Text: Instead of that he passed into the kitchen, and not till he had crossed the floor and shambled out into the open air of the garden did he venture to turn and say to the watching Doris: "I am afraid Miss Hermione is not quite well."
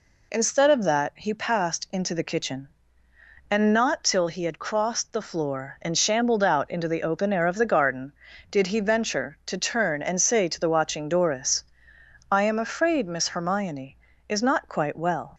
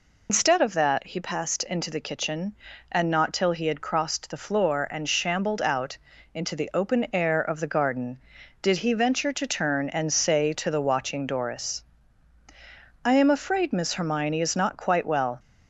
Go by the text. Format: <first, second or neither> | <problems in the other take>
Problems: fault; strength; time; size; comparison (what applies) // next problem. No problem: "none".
first | loses the start of "Instead"; at 0.2 s; 130 ms // pauses between "out" and "into"; at 5.9 s; 0.38 s long